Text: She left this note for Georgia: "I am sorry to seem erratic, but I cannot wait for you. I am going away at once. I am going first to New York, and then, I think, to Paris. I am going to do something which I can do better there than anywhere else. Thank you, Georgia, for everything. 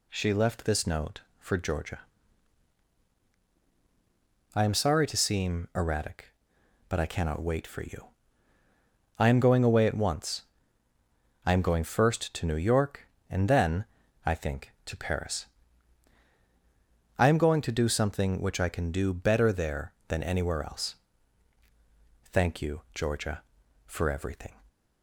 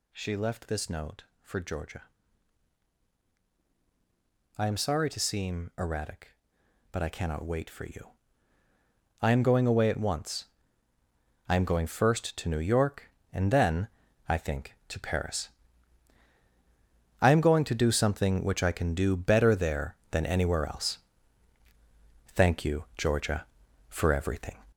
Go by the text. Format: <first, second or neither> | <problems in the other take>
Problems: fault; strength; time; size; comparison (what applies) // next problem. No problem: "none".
first | gets louder; throughout; 6 dB